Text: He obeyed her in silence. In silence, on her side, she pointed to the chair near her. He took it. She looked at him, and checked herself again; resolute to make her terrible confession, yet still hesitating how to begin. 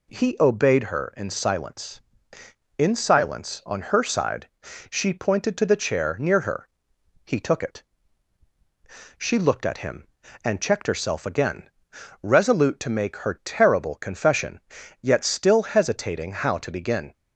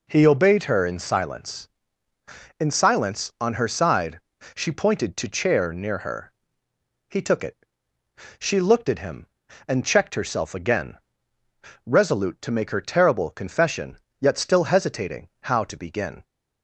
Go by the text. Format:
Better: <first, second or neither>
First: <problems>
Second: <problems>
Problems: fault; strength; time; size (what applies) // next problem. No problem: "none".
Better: first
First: none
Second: skips "the"; at 5.2 s